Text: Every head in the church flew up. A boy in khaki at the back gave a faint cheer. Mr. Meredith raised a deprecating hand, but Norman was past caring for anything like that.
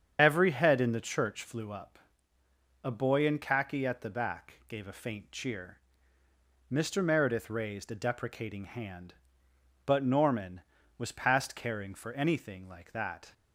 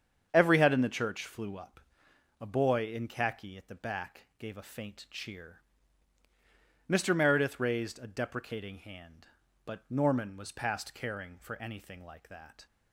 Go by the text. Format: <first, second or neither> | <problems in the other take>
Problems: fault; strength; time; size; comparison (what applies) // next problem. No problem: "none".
second | loses the start of "Every"; at 0.1 s; 40 ms // starts louder than the rest; strong; until 1.2 s; 8 dB; strong in the second